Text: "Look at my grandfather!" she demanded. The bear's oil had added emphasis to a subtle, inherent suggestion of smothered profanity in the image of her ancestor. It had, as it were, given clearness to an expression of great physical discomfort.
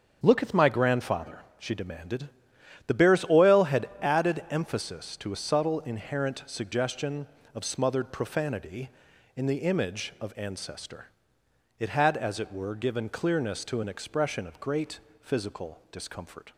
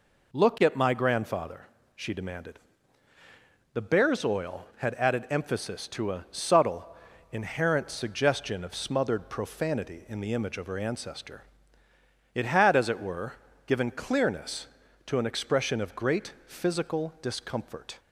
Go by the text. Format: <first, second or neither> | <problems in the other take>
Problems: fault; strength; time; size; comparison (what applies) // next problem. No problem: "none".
second | starts louder than the rest; until 1.2 s; 7 dB // skips "her"; at 10.3 s // pauses between "great" and "physical"; slight; at 14.9 s; 0.22 s long